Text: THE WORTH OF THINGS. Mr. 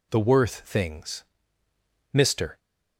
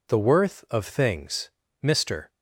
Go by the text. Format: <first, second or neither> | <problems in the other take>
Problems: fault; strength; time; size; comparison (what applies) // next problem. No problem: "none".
second | skips "OF"; at 0.6 s